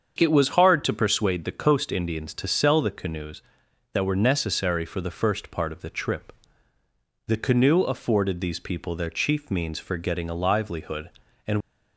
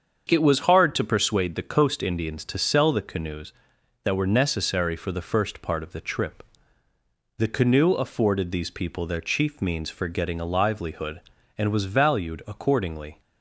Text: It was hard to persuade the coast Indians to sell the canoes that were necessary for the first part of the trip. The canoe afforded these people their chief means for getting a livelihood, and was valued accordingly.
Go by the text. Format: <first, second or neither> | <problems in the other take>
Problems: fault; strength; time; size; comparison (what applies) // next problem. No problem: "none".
second | starts louder than the rest; until 1.2 s; 7 dB; also in the second // stops before "was valued accordingly"; at 11.6 s